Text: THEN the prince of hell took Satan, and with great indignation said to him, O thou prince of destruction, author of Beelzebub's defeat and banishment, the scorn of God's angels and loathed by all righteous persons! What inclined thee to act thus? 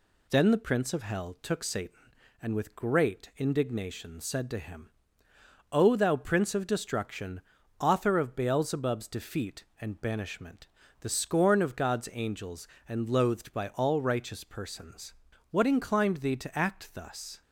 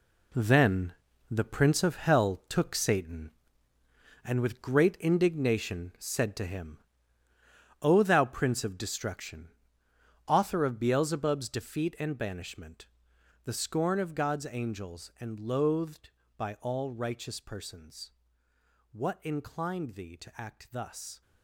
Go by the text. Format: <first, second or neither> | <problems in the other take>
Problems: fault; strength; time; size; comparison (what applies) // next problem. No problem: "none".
first | gets quieter; strong; throughout; 11 dB // pauses between "THEN" and "the"; at 0.9 s; 0.38 s long